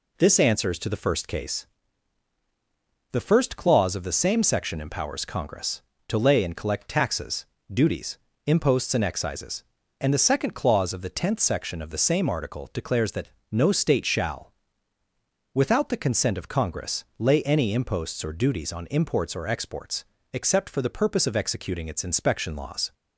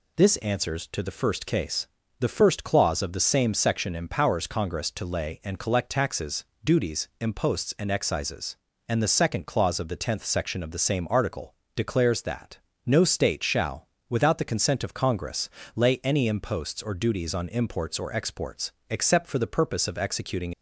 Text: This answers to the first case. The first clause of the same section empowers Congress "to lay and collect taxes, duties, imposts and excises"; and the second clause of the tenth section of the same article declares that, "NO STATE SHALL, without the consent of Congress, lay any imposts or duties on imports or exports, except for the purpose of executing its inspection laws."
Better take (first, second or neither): first